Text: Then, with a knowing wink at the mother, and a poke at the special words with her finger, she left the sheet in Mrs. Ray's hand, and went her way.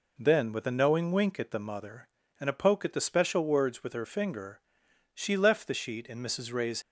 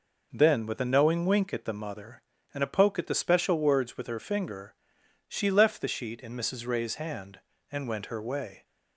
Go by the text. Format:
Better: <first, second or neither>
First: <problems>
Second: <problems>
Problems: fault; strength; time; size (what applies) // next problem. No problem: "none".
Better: second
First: stops before "hand and went her way"; at 6.8 s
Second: none